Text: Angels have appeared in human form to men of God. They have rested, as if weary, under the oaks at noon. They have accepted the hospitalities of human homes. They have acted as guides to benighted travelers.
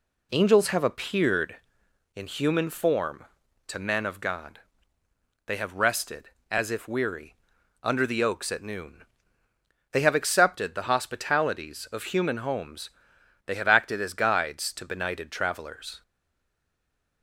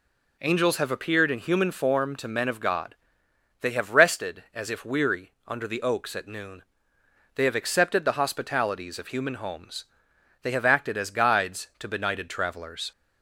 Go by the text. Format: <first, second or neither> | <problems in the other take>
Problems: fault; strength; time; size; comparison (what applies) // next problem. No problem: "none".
second | stays silent after the last word; noticeable; from 16.0 s on; 1.2 s long